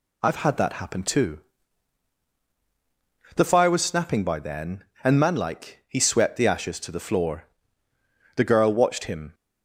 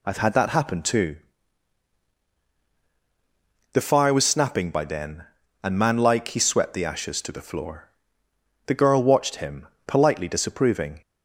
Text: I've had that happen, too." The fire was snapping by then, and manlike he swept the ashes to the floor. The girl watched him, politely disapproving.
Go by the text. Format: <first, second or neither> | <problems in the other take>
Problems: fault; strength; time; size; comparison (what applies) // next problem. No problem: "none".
second | stops before "politely disapproving"; at 9.3 s